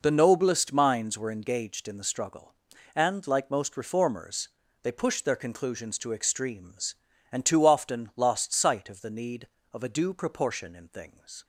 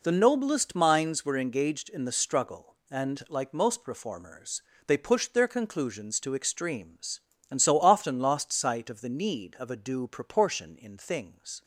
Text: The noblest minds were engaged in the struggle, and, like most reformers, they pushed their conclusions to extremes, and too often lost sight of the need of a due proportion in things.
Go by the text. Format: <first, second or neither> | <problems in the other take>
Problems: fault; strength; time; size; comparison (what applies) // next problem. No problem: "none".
first | says "so" for "too"; at 7.6 s